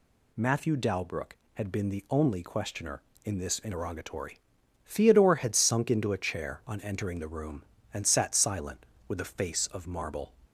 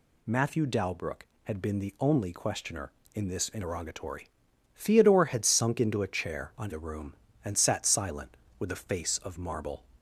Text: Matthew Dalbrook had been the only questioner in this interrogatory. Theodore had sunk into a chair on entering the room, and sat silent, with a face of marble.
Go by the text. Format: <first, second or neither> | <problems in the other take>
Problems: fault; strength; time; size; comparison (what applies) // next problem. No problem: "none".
first | skips "entering"; at 6.7 s